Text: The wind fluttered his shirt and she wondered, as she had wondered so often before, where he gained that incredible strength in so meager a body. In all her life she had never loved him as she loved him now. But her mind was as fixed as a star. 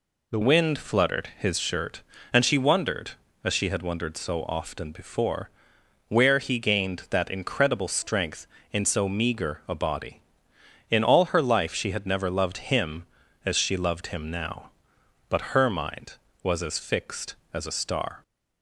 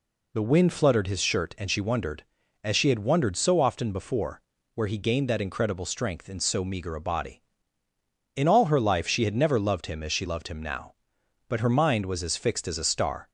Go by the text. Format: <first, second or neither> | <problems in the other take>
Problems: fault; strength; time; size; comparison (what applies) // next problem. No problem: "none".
second | changes voice at "wind"; from 0.4 s on; 17.8 s long